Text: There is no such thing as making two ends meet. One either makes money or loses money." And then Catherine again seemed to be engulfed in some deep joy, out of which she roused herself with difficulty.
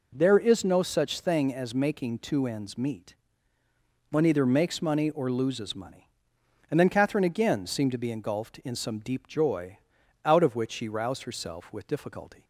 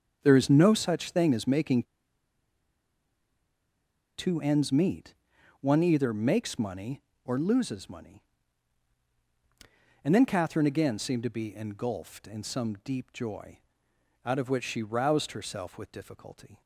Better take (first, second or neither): first